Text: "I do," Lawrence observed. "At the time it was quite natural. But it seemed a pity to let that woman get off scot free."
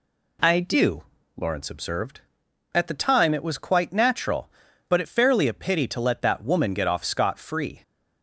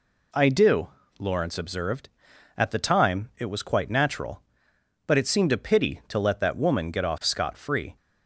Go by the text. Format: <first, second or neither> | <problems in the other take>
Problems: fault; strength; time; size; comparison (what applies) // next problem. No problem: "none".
second | says "fairly" for "seemed"; at 5.0 s